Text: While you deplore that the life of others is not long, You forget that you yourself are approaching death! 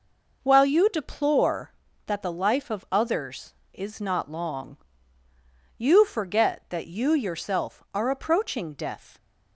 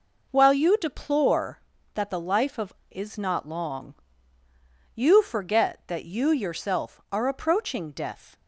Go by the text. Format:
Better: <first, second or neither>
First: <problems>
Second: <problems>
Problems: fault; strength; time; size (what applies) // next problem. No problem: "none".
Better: first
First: none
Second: skips "others"; at 2.8 s